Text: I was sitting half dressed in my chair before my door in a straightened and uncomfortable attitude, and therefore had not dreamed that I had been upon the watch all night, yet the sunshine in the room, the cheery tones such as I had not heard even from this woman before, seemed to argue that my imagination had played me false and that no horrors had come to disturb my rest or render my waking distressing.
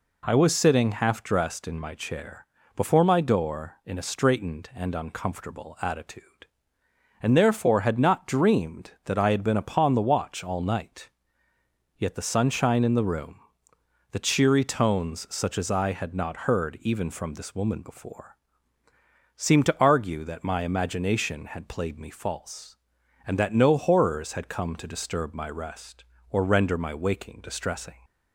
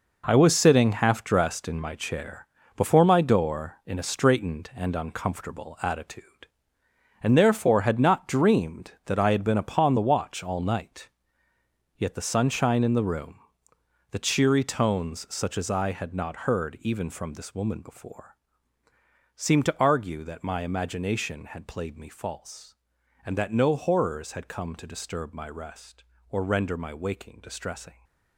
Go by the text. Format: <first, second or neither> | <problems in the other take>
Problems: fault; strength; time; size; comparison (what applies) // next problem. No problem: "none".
first | gets quieter; strong; throughout; 10 dB // pauses between "chair" and "before"; slight; at 2.4 s; 0.30 s long; slight in the first